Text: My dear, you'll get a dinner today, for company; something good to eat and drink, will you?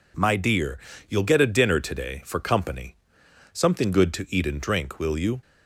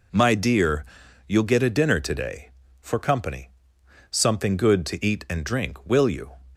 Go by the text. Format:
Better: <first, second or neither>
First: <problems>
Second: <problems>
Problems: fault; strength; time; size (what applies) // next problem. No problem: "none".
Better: neither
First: none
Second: none